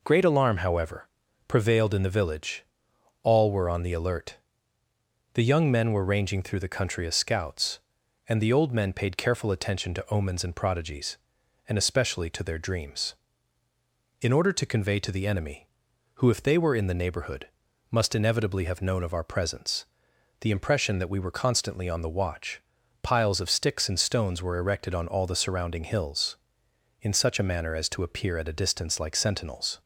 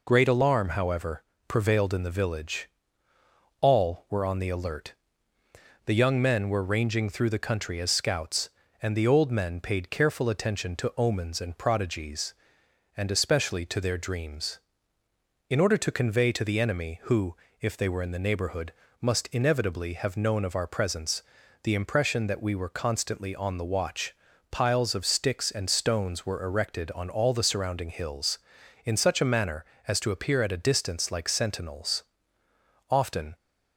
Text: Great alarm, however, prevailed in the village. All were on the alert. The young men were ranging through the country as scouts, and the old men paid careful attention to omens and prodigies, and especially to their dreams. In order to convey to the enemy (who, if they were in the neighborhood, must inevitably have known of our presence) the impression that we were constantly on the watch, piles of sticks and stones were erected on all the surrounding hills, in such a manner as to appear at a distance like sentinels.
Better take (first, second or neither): first